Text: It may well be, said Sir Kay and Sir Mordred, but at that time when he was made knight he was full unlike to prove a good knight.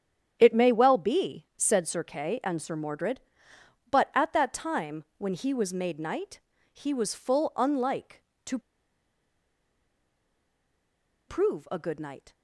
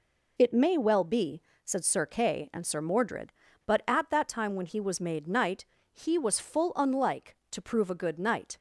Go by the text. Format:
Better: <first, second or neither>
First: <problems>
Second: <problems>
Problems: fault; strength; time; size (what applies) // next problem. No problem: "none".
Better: second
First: starts louder than the rest; strong; until 1.4 s; 9 dB // pauses between "knight" and "he"; slight; at 6.3 s; 0.34 s long // pauses between "to" and "prove"; strong; at 8.5 s; 2.6 s long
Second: pauses between "knight" and "he"; slight; at 5.6 s; 0.26 s long